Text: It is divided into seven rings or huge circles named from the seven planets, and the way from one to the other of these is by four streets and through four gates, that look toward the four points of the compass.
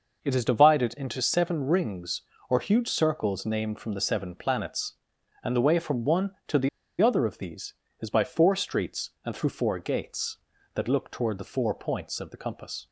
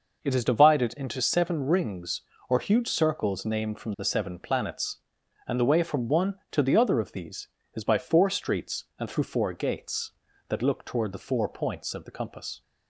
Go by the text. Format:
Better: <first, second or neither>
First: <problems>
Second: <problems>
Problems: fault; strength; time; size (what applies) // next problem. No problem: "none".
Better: second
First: pauses between "the" and "other"; slight; at 6.6 s; 0.32 s long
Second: none